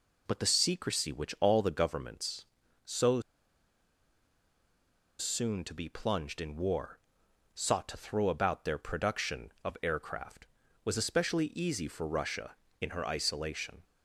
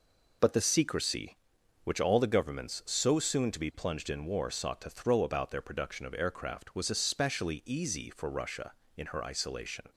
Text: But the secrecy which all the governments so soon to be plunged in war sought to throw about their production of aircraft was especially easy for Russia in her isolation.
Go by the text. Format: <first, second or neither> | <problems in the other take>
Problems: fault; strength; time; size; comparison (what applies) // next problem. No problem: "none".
second | pauses between "so" and "soon"; strong; at 3.2 s; 1.9 s long // pauses between "war" and "sought"; noticeable; at 6.9 s; 0.56 s long